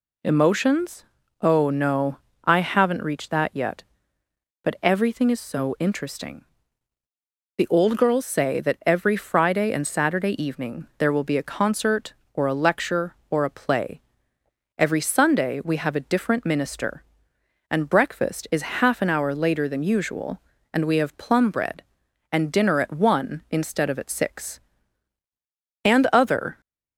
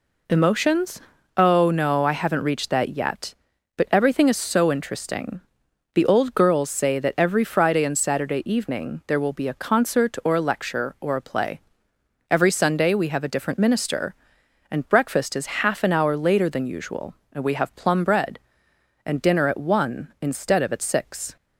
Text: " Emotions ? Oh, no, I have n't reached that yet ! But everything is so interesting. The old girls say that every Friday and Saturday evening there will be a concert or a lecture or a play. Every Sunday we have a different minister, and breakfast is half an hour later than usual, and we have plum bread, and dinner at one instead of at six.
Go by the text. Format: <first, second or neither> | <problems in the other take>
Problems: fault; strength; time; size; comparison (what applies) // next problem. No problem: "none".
second | goes on to say "And other"; noticeable; from 25.8 s on; 0.78 s long